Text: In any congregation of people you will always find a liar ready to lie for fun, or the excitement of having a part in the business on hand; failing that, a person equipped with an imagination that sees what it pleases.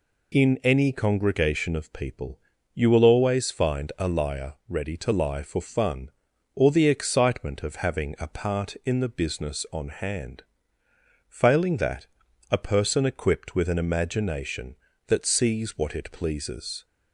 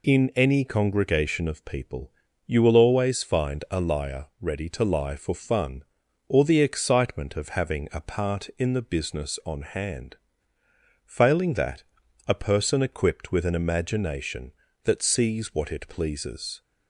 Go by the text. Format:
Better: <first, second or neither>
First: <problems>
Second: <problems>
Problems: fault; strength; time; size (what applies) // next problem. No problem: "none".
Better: neither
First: pauses between "people" and "you"; slight; at 2.3 s; 0.34 s long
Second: pauses between "people" and "you"; slight; at 2.1 s; 0.34 s long